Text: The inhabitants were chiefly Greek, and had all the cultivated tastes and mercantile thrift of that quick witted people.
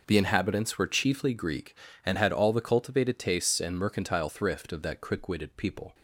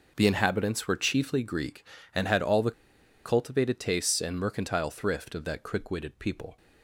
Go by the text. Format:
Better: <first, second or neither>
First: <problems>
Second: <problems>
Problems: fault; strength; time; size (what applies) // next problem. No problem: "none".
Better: first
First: none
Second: pauses between "the" and "cultivated"; noticeable; at 2.7 s; 0.53 s long